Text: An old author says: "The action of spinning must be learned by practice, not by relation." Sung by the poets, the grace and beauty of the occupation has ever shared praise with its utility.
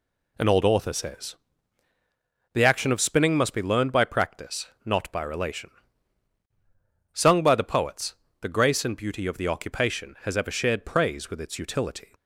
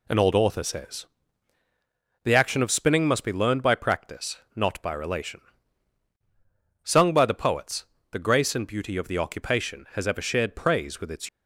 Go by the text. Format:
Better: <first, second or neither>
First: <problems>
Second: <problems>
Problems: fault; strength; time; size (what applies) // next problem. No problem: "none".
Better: first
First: none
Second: stops before "utility"; at 11.2 s